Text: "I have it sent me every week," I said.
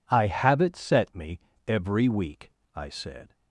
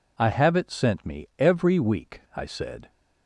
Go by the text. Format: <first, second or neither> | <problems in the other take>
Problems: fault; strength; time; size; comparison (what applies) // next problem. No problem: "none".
second | says "set" for "sent"; at 0.7 s // pauses between "me" and "every"; slight; at 1.3 s; 0.28 s long